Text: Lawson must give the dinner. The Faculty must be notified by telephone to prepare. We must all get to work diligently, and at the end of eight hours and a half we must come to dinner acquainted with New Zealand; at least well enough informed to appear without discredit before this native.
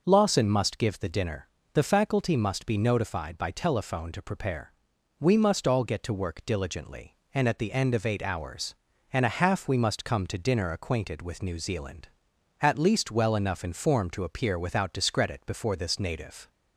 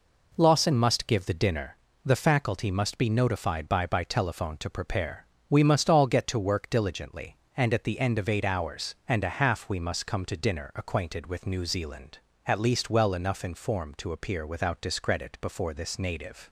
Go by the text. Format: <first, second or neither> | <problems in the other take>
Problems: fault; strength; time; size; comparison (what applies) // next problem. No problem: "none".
first | says "by" twice; at 3.8 s